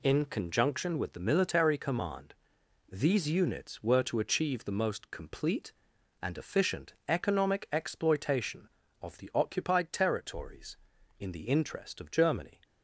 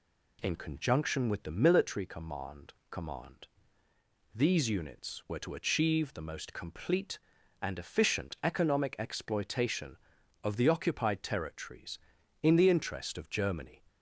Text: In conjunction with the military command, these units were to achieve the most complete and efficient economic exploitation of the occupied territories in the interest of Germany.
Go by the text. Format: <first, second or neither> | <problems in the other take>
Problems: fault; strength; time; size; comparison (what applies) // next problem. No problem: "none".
first | says "command" twice; at 2.8 s